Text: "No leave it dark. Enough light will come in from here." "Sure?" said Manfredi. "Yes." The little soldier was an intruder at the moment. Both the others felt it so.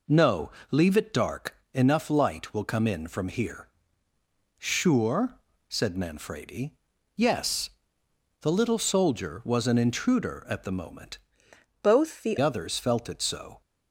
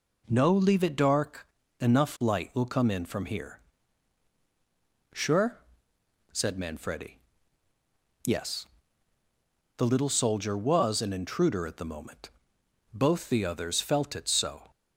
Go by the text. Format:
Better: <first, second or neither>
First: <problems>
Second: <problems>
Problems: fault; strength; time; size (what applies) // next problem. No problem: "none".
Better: second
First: pauses between "No" and "leave"; slight; at 0.5 s; 0.18 s long // changes voice from "Both" to "the"; from 11.8 to 12.3 s; 0.5 s long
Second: none